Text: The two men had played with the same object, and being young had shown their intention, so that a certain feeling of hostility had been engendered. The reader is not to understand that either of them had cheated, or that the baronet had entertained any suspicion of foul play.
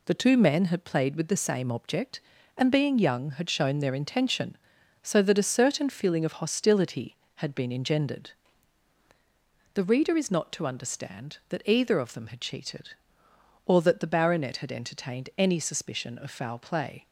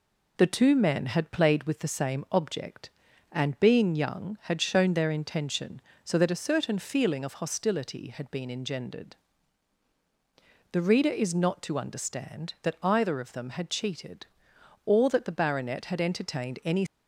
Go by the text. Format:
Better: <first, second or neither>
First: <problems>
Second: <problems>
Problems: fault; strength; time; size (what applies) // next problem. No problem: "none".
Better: first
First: none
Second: stops before "suspicion of foul play"; at 16.8 s